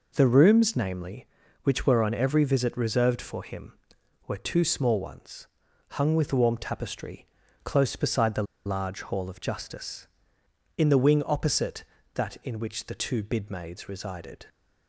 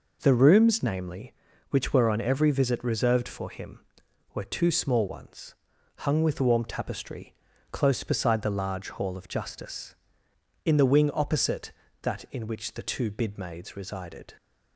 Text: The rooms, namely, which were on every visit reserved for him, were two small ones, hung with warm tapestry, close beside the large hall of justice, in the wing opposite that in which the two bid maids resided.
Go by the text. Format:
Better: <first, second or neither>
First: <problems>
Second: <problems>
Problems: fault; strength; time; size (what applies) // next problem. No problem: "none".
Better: second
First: pauses between "the" and "large"; slight; at 8.4 s; 0.22 s long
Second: none